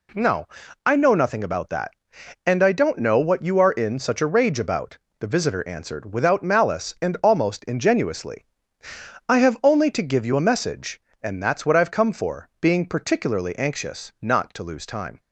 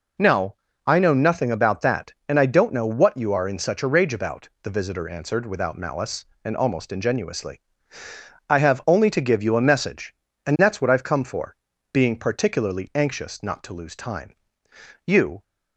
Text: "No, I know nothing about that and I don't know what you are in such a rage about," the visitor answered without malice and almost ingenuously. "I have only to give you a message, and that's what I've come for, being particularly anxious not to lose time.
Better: first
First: none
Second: goes on to say "You"; slight; from 15.0 s on; 0.38 s long

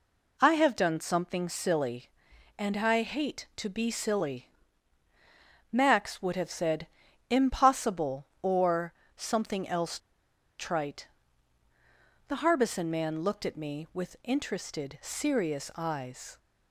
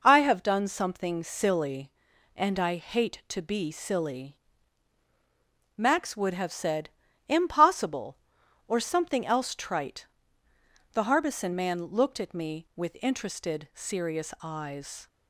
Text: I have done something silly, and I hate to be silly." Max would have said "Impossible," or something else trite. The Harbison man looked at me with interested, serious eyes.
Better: second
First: pauses between "said" and "Impossible"; at 6.8 s; 0.42 s long // pauses between "or" and "something"; slight; at 8.9 s; 0.22 s long // pauses between "else" and "trite"; noticeable; at 9.9 s; 0.61 s long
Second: pauses between "said" and "Impossible"; at 6.8 s; 0.40 s long

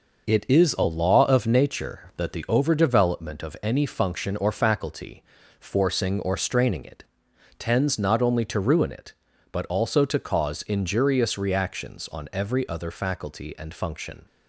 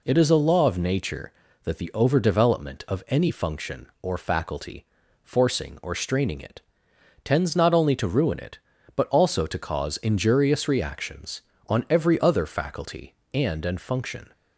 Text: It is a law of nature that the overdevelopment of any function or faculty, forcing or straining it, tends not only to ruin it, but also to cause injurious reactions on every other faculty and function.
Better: first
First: none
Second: says "and" twice; at 13.6 s

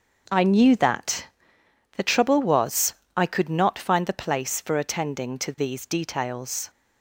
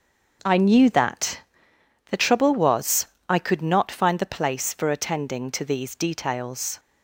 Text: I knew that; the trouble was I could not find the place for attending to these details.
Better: neither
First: starts louder than the rest; until 1.9 s; 6 dB // pauses between "was" and "I"; slight; at 2.9 s; 0.20 s long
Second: starts louder than the rest; until 2.1 s; 6 dB // pauses between "was" and "I"; slight; at 3.0 s; 0.20 s long

